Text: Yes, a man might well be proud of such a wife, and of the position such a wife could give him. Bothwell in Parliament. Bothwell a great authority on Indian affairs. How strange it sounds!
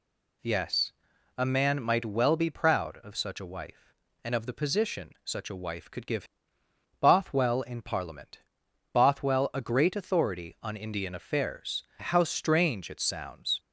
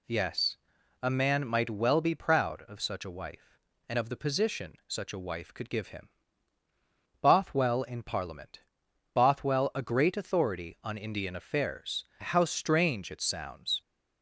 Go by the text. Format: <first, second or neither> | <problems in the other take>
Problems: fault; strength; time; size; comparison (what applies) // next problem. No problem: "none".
second | skips "him"; at 6.6 s